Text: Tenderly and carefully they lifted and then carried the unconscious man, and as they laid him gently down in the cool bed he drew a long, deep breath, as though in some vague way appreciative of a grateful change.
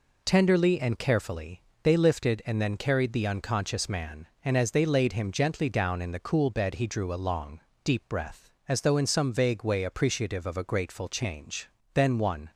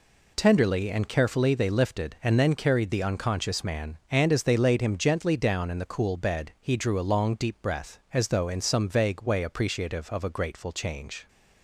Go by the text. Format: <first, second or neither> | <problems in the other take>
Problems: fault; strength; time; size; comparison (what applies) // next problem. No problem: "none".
second | pauses between "carefully" and "they"; slight; at 1.6 s; 0.20 s long // goes on to say "Then one"; from 11.9 s on; 0.56 s long